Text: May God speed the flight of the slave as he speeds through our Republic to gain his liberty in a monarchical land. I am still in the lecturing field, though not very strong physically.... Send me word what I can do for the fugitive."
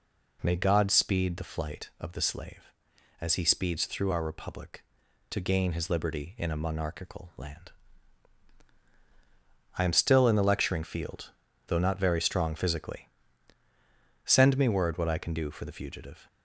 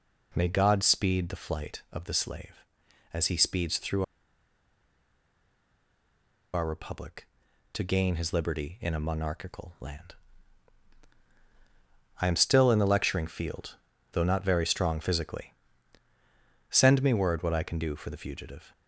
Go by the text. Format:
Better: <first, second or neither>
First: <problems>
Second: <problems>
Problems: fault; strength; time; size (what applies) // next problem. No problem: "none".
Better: first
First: none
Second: pauses between "through" and "our"; strong; at 4.0 s; 2.5 s long